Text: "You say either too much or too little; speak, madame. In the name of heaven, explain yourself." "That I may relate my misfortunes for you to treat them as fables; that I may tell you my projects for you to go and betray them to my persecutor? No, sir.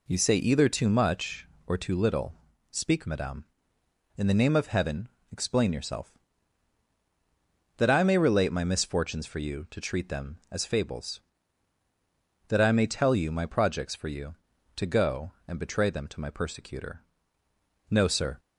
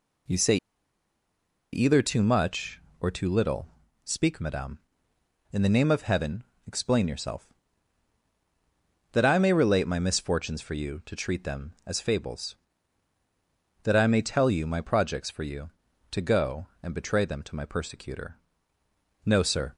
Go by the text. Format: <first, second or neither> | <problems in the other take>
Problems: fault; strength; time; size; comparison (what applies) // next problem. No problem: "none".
first | pauses between "say" and "either"; at 0.5 s; 1.1 s long